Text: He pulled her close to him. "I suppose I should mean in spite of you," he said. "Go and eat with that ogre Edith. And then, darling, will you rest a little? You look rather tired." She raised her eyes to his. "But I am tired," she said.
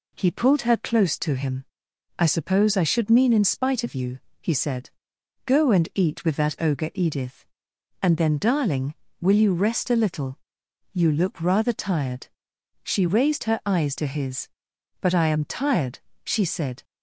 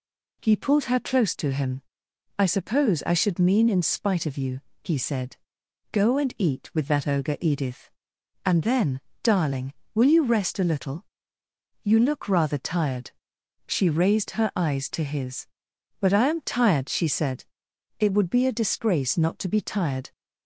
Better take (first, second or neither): first